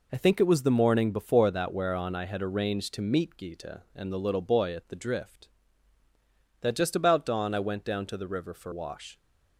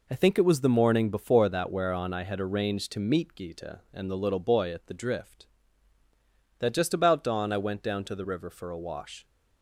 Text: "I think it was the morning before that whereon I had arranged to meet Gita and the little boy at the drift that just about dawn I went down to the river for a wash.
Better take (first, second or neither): second